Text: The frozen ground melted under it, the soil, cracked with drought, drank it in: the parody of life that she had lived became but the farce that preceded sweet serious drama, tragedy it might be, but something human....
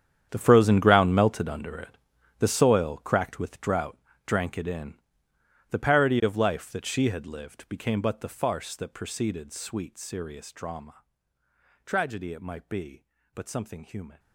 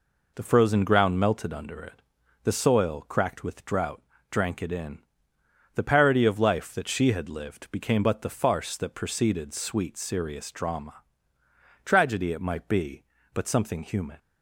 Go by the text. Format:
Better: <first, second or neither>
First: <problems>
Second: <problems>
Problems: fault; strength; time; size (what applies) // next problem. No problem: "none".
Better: second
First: gets quieter; strong; throughout; 17 dB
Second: none